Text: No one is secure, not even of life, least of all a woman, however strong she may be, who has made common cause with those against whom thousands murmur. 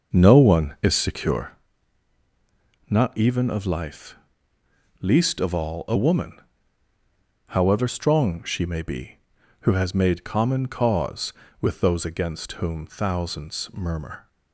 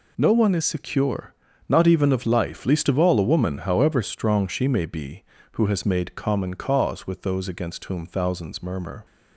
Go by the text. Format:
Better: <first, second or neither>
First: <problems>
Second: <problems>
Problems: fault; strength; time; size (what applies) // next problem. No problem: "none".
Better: second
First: starts louder than the rest; noticeable; until 1.6 s; 6 dB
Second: none